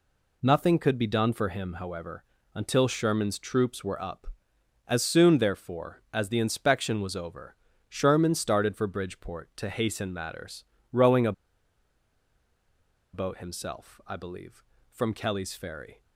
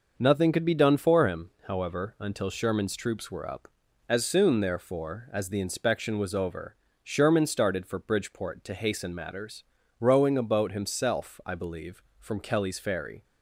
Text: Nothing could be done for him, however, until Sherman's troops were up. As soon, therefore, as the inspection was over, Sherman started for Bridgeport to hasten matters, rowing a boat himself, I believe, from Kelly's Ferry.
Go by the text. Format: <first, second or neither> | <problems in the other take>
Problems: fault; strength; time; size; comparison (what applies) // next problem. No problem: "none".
second | pauses between "a" and "boat"; strong; at 11.3 s; 1.8 s long